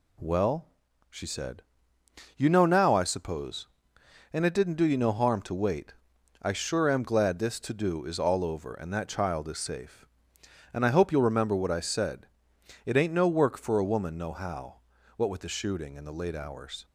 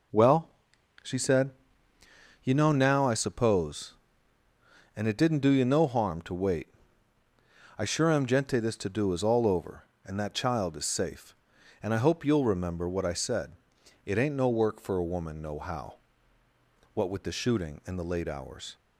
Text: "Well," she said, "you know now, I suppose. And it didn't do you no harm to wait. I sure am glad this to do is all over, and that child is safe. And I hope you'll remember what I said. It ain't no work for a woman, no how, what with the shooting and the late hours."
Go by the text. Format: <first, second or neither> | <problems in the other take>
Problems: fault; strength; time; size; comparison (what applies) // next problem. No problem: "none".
first | says "gente" for "glad"; at 8.2 s